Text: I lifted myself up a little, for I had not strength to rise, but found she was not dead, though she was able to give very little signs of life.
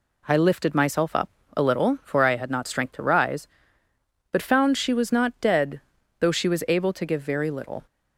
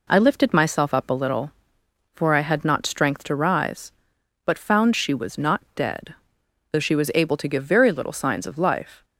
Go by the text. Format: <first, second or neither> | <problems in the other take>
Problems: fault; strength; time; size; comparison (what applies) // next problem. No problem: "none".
second | pauses between "up" and "a"; slight; at 1.2 s; 0.26 s long // stops before "signs of life"; at 7.8 s